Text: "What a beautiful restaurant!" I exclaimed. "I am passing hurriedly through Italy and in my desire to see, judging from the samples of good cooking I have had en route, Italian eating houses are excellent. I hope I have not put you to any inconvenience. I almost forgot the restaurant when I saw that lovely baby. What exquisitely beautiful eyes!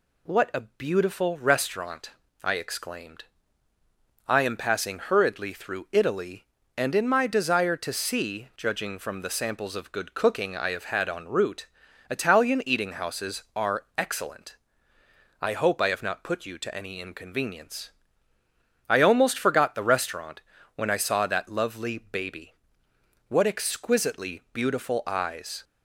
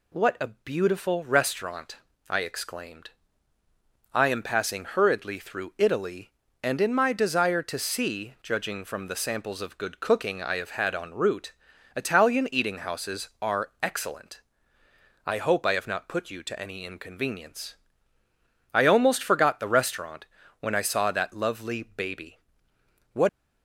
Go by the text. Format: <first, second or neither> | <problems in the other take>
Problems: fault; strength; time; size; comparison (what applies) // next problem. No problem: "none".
first | pauses between "restaurant" and "when"; slight; at 20.2 s; 0.34 s long; slight in the first // stops before "exquisitely beautiful eyes"; at 23.2 s